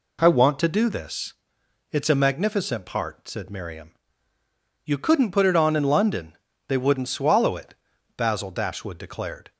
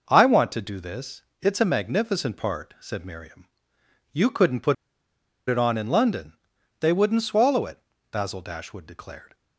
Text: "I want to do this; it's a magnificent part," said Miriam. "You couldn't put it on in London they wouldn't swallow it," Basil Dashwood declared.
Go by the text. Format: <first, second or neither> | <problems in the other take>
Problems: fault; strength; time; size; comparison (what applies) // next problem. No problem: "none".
first | pauses between "put" and "it"; noticeable; at 4.7 s; 0.74 s long // pauses between "London" and "they"; noticeable; at 6.3 s; 0.48 s long; slight in the first